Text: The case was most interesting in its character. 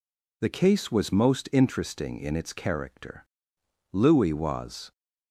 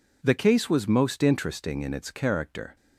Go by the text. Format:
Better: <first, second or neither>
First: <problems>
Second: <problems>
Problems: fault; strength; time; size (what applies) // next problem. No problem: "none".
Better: second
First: goes on to say "Louis was"; noticeable; from 3.9 s on; 0.98 s long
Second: none